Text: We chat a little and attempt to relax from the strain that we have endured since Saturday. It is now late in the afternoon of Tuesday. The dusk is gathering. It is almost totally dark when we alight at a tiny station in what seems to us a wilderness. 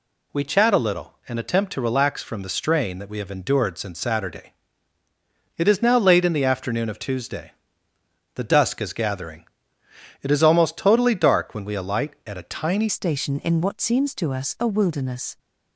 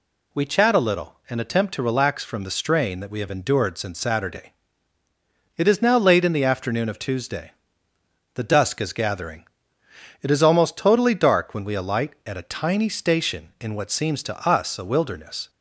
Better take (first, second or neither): second